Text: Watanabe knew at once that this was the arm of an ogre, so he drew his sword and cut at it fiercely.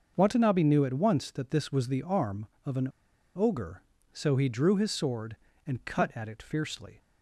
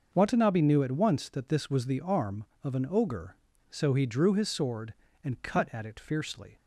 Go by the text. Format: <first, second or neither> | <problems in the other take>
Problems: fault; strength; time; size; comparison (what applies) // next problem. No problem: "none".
second | starts louder than the rest; noticeable; until 1.1 s; 6 dB; noticeable in the second // pauses between "an" and "ogre"; noticeable; at 2.8 s; 0.48 s long